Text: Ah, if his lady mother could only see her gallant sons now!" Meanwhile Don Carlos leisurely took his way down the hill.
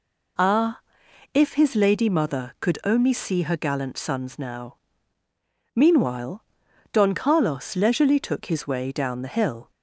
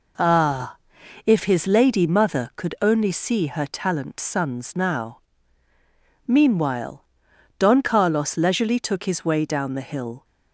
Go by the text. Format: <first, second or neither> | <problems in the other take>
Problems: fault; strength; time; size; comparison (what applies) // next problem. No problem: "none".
first | says "talent" for "gallant"; at 3.6 s // pauses between "Meanwhile" and "Don"; noticeable; at 7.0 s; 0.54 s long; noticeable in the first